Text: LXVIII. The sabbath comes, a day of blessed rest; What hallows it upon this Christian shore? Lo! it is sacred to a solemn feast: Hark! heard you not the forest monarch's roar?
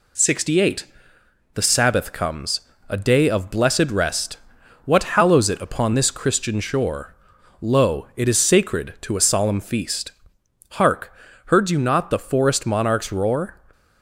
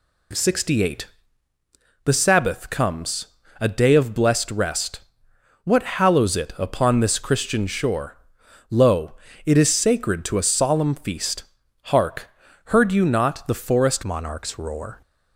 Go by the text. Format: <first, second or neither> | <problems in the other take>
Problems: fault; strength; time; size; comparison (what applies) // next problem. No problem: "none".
first | changes voice at "monarch's"; from 14.0 s on; 1.0 s long